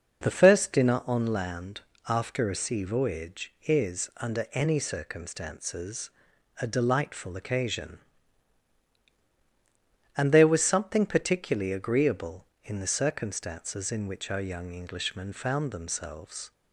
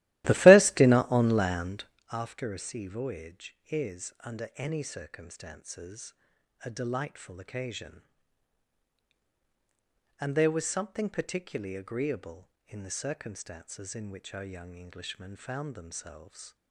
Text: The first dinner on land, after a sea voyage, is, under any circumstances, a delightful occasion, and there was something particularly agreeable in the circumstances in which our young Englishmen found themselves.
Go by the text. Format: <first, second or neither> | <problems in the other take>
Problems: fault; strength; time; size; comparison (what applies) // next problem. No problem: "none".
first | starts louder than the rest; strong; until 2.0 s; 16 dB